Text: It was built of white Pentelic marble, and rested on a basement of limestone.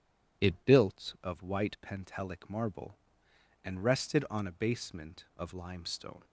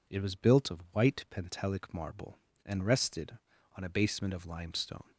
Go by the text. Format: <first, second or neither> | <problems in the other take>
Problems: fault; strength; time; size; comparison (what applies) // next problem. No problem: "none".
second | skips "was"; at 0.6 s